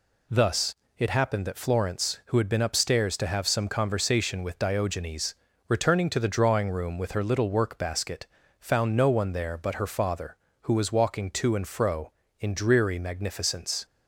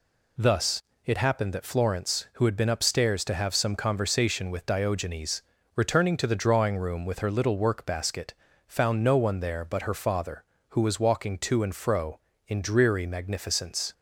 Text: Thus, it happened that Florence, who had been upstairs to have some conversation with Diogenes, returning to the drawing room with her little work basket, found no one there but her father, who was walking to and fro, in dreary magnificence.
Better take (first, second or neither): neither